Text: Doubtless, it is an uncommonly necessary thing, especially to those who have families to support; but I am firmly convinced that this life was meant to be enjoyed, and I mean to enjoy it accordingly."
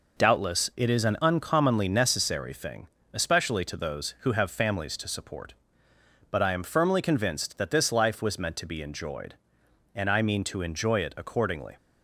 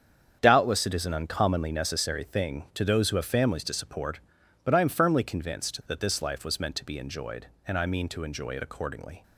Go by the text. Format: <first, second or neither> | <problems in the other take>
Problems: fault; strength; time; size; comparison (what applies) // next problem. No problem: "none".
first | starts louder than the rest; strong; until 1.4 s; 8 dB // skips "especially"; at 2.6 s